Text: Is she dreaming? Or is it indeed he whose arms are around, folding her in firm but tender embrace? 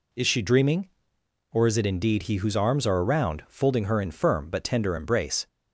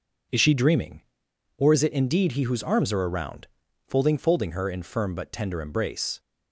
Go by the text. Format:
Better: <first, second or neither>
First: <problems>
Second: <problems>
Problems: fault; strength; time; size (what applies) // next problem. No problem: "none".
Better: first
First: none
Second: says "folding" twice; at 4.1 s